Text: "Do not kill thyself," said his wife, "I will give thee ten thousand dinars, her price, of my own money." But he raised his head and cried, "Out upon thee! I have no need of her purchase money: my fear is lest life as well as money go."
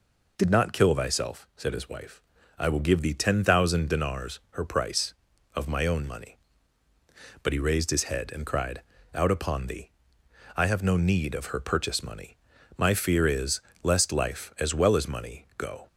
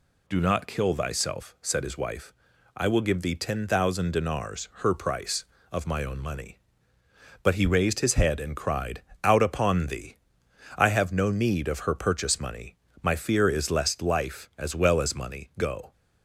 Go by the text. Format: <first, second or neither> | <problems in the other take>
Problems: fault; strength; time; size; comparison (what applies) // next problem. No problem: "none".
second | says "Did" for "Do"; at 0.3 s // pauses between "is" and "lest"; slight; at 13.6 s; 0.20 s long